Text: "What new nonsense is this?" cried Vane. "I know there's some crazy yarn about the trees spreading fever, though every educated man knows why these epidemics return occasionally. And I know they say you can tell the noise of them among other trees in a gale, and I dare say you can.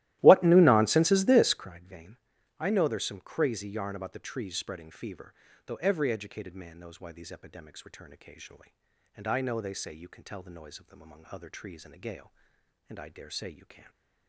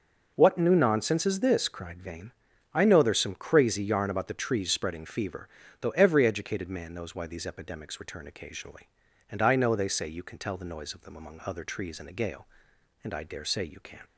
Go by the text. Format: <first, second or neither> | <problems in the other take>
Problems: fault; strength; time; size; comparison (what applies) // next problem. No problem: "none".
second | starts louder than the rest; strong; until 1.7 s; 15.5 dB